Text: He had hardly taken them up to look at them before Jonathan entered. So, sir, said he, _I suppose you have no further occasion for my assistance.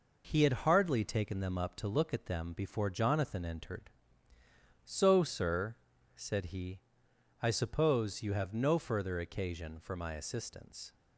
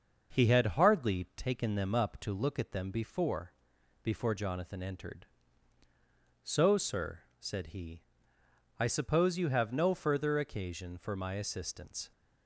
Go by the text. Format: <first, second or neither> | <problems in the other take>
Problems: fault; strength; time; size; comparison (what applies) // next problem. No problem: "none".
first | starts louder than the rest; until 1.4 s; 6 dB // says "before" twice; at 4.0 s